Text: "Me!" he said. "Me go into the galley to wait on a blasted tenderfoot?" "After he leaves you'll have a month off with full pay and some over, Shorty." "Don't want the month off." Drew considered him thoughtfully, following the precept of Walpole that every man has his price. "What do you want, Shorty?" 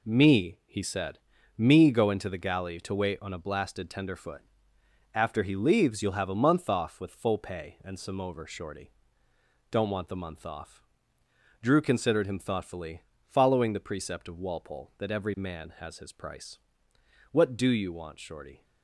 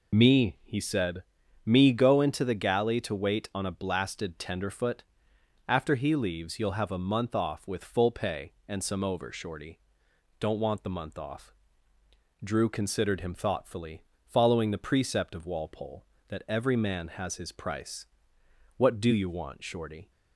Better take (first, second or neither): first